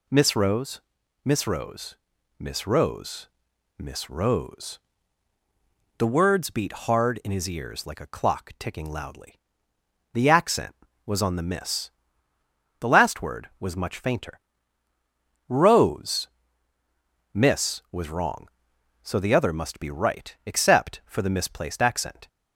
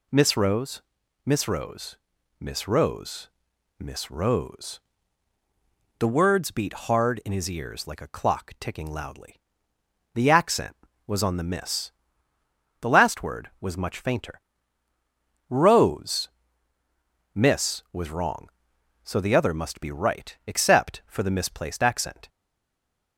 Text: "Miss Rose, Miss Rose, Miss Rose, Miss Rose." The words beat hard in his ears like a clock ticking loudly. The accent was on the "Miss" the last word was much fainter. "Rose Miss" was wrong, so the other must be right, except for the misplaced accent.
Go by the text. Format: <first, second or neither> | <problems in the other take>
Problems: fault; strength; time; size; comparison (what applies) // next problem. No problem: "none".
first | pauses between "Miss" and "the"; noticeable; at 11.9 s; 0.90 s long; noticeable in the first // pauses between "Rose" and "Miss"; at 16.2 s; 1.0 s long; also in the first // stays silent after the last word; slight; from 22.2 s on; 0.9 s long